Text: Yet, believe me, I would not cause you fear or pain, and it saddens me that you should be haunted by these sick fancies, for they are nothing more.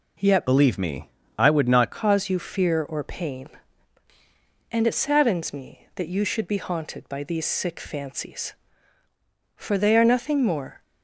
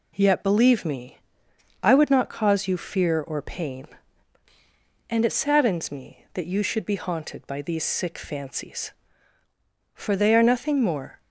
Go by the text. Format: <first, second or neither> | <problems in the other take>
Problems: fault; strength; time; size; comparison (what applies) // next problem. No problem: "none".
second | changes voice from "believe" to "not"; from 0.4 to 1.9 s; 1.5 s long